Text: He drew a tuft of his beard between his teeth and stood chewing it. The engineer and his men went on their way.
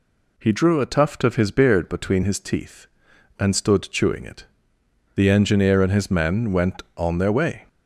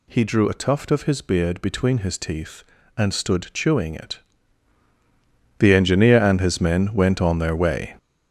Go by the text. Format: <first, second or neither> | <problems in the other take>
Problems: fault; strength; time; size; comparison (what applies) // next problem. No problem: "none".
first | gets louder; strong; throughout; 7.5 dB